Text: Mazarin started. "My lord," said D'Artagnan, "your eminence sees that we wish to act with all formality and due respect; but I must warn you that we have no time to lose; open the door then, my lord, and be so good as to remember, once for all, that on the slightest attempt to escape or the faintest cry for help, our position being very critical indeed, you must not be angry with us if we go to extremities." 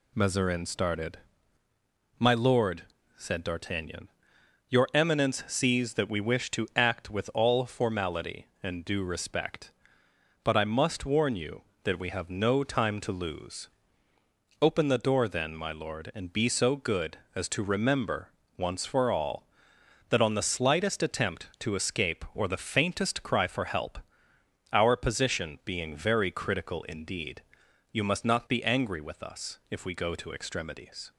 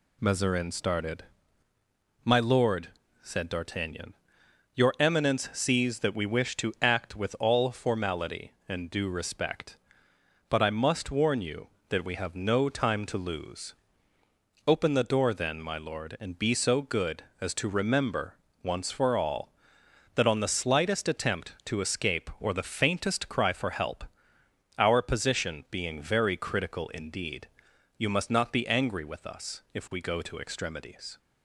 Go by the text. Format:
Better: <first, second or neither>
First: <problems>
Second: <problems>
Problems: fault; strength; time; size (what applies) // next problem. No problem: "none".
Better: neither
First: none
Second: none